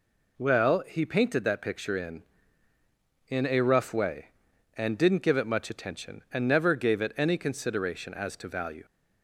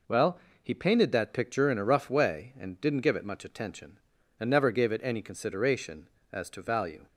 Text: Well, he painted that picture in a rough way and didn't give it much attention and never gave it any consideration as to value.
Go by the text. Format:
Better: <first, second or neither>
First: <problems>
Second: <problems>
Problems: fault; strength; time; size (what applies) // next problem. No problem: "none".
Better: second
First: says "in" twice; at 3.2 s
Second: none